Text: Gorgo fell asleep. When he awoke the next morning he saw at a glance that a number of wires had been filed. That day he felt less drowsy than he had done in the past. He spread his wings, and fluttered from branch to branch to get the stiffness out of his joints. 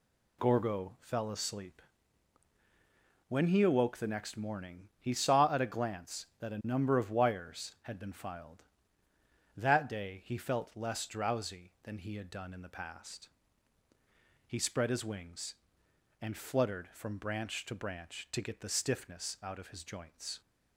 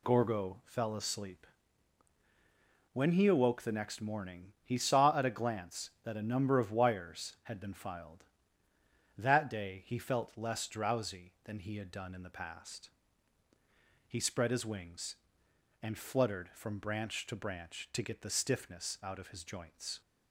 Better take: neither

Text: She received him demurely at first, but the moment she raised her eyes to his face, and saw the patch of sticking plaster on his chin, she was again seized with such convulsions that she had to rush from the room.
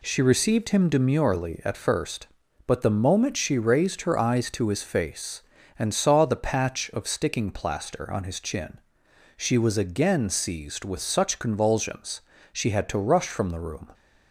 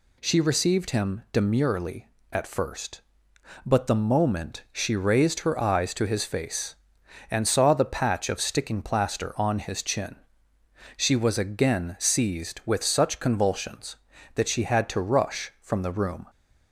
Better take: second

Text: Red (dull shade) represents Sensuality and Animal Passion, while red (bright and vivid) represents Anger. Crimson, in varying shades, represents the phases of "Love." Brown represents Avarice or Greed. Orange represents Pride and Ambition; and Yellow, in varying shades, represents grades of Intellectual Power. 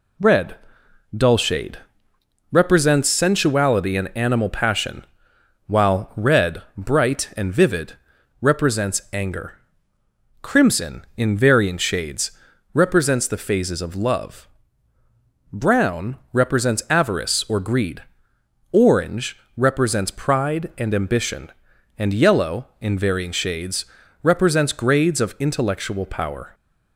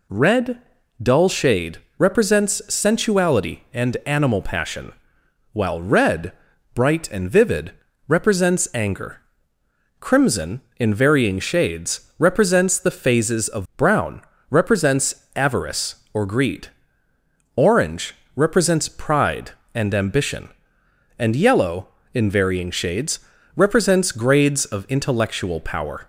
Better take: first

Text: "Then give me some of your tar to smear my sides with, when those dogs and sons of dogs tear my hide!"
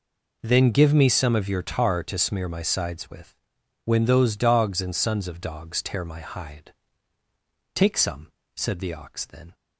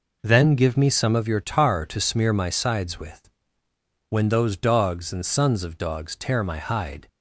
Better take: second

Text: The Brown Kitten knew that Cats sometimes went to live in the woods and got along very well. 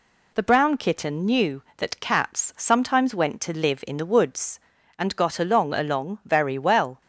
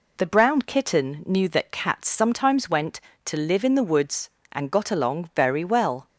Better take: second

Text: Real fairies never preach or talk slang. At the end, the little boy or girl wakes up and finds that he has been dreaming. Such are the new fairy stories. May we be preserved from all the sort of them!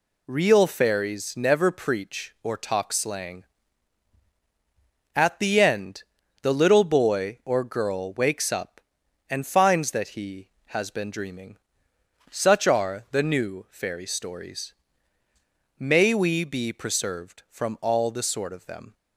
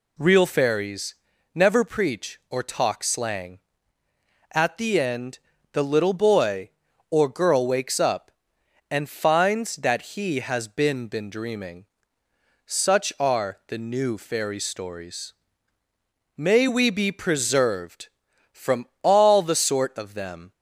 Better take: first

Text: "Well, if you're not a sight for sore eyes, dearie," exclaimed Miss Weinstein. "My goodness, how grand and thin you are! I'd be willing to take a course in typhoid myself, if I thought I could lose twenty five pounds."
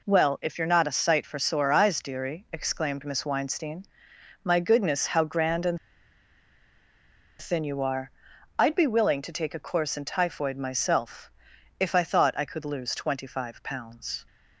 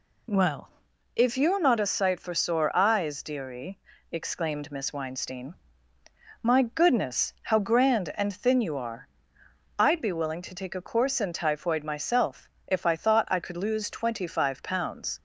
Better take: second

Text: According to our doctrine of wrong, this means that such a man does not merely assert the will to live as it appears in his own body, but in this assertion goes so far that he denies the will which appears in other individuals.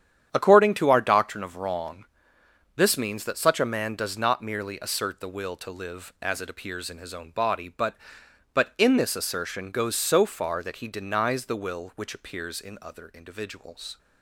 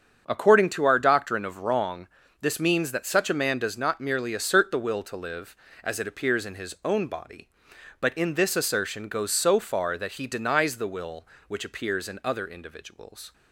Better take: second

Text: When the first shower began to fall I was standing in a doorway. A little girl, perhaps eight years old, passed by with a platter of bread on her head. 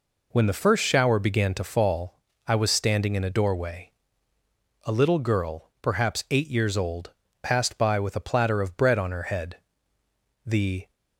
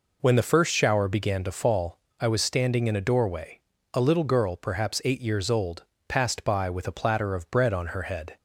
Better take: second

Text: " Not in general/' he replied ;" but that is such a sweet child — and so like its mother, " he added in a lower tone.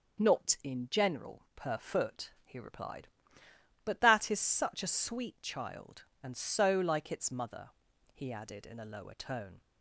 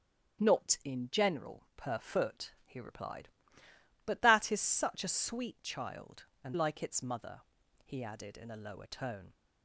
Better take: first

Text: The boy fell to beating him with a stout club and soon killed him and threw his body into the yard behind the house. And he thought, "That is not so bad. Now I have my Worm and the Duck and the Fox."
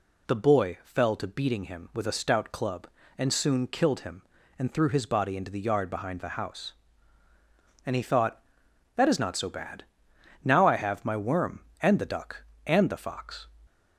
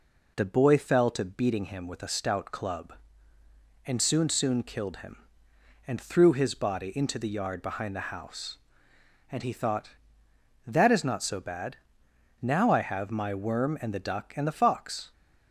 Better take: first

